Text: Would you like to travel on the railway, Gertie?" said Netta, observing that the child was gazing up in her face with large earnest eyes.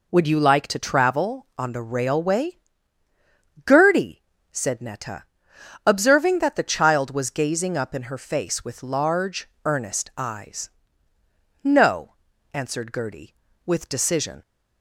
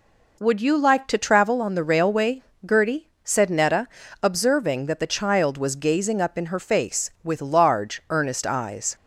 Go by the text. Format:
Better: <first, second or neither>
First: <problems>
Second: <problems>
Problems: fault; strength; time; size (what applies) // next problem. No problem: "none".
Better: second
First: pauses between "large" and "earnest"; slight; at 9.4 s; 0.18 s long // goes on to say "No answered Gertie with decision"; strong; from 11.6 s on; 2.8 s long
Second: none